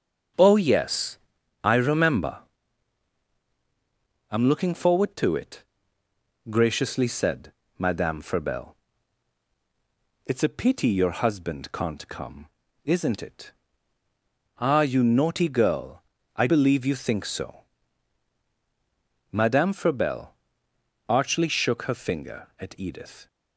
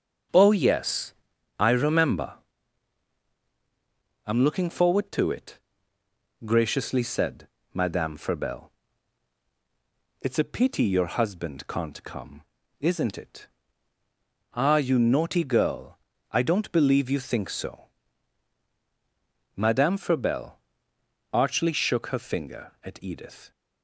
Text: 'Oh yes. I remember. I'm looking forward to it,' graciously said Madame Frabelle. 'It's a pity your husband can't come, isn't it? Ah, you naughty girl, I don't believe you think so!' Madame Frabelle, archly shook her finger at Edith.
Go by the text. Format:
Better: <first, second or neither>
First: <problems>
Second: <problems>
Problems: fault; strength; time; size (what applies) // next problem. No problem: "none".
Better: second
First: starts louder than the rest; until 1.8 s; 7 dB // pauses between "said" and "Madame"; slight; at 7.5 s; 0.26 s long // skips "don't"; at 16.4 s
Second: starts louder than the rest; until 1.7 s; 7 dB // pauses between "said" and "Madame"; slight; at 7.4 s; 0.26 s long